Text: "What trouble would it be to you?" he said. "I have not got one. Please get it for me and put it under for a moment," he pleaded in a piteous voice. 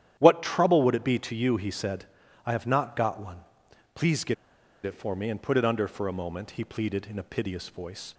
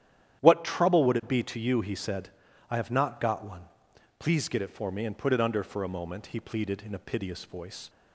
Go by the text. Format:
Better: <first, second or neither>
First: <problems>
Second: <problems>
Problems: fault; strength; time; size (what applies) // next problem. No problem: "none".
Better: second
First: starts louder than the rest; strong; until 1.2 s; 10.5 dB // pauses between "get" and "it"; noticeable; at 4.3 s; 0.50 s long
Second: starts louder than the rest; strong; until 1.4 s; 10.5 dB